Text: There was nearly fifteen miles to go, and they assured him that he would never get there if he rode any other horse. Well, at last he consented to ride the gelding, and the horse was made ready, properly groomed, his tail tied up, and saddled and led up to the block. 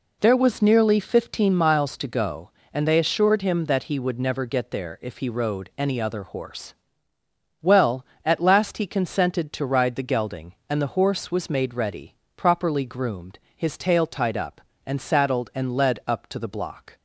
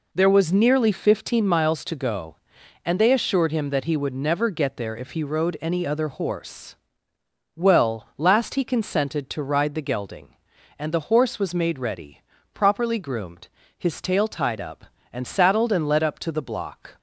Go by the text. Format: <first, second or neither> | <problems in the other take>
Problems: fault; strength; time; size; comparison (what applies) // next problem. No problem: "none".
first | skips "at"; at 8.1 s